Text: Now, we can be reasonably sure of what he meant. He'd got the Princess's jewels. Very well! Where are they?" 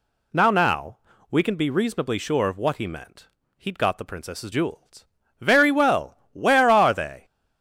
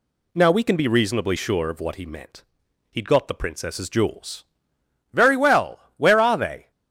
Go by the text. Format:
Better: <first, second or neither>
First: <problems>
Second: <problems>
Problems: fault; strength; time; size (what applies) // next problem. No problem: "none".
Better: second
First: says "Now" twice; at 0.5 s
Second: none